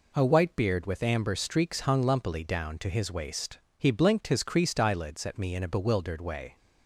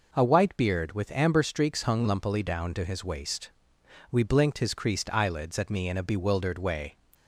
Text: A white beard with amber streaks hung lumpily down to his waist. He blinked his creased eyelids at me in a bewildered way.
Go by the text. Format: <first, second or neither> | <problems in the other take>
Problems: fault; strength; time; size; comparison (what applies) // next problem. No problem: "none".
first | says "We" for "He"; at 4.1 s